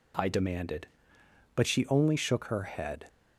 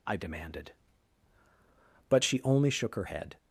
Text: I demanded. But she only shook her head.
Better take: first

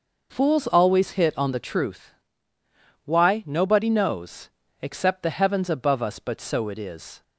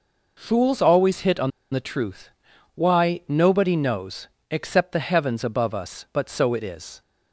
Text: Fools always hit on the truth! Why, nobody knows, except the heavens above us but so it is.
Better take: first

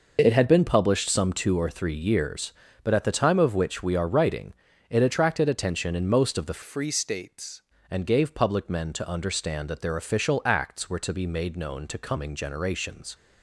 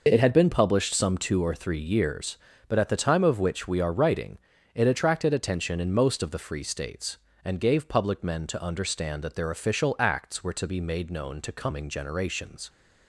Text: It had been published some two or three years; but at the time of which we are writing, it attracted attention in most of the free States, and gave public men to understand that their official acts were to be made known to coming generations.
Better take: second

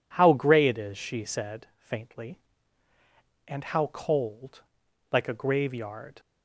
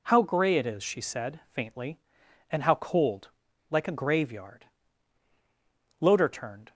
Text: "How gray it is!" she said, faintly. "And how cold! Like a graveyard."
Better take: first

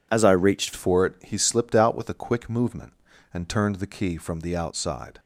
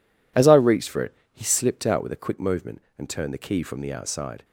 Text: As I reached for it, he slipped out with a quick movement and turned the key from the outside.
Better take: second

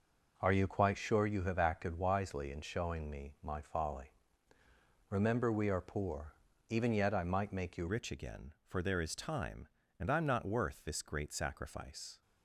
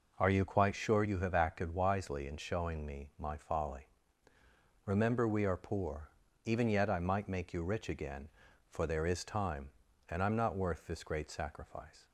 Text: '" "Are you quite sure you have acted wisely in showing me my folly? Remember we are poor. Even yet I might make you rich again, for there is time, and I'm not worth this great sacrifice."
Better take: second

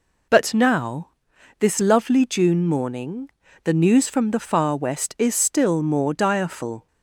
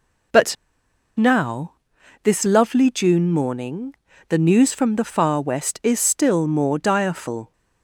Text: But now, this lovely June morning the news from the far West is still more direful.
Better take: first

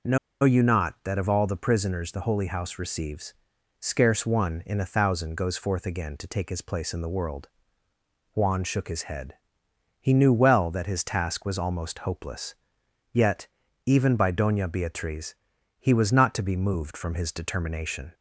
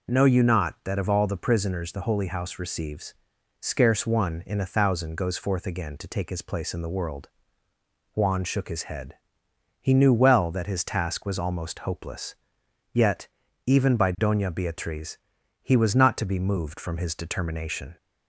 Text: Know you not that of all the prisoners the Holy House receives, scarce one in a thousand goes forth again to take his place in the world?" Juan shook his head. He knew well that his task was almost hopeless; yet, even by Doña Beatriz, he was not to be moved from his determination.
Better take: second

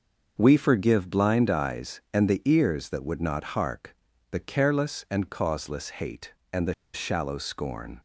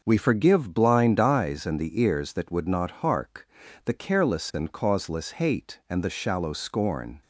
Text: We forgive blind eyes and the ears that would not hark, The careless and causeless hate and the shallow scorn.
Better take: second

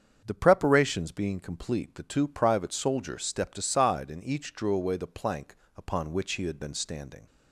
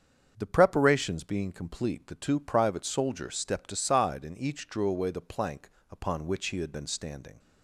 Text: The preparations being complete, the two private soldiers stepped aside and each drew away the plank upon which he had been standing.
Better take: neither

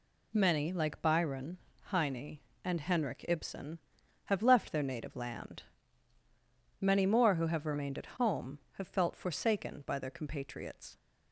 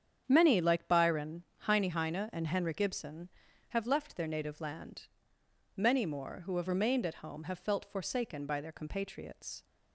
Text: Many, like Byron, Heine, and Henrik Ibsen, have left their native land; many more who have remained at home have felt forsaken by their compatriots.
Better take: first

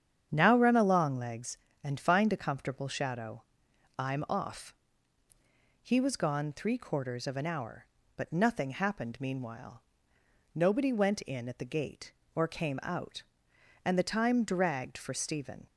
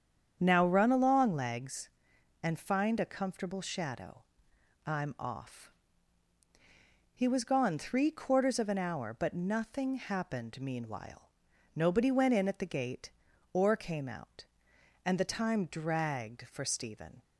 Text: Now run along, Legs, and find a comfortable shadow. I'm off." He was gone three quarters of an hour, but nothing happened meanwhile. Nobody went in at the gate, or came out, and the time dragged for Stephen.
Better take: neither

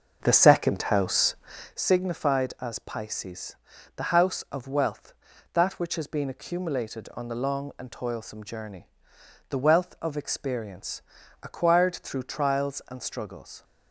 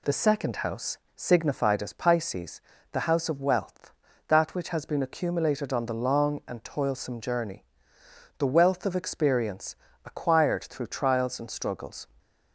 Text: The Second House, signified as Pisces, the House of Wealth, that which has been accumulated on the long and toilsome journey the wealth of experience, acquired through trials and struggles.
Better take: second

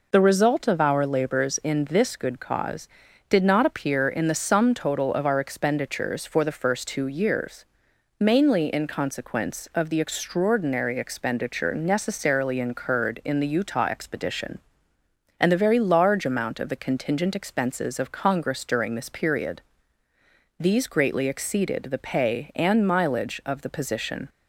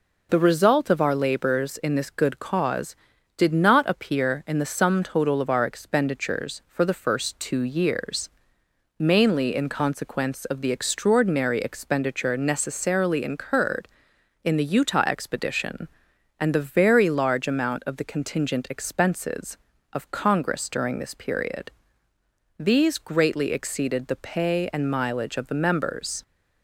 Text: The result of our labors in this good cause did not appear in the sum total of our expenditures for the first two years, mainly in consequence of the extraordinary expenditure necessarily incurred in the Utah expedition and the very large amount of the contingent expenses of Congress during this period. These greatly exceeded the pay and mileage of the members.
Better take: second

